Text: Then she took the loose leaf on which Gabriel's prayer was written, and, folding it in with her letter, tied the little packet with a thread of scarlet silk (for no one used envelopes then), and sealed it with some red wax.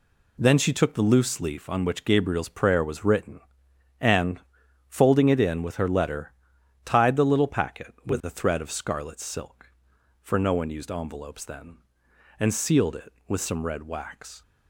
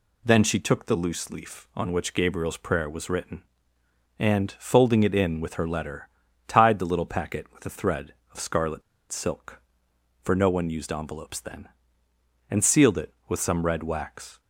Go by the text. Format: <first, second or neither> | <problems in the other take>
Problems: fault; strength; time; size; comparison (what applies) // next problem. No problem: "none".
first | pauses between "scarlet" and "silk"; slight; at 8.8 s; 0.29 s long